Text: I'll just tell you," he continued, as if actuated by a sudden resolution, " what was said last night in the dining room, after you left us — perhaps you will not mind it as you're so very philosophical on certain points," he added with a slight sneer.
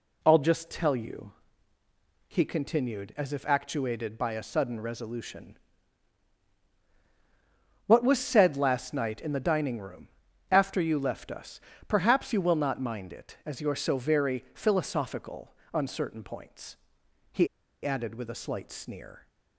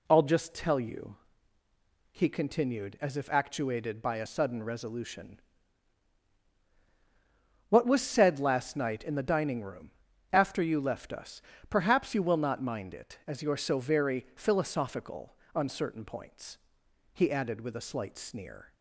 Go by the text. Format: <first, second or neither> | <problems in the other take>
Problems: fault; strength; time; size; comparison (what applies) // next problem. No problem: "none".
second | pauses between "he" and "added"; at 17.4 s; 0.37 s long